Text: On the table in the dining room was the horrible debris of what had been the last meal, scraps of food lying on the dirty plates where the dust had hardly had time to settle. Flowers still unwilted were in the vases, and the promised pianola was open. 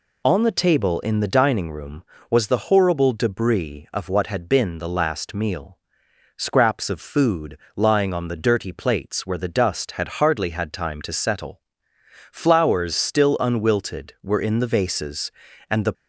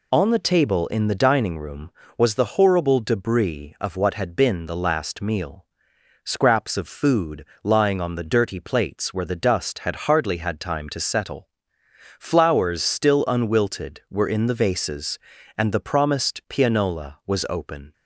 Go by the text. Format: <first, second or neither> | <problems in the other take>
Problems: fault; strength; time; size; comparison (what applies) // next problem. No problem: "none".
second | pauses between "food" and "lying"; slight; at 7.5 s; 0.20 s long; slight in the second // stops before "promised pianola was open"; at 15.9 s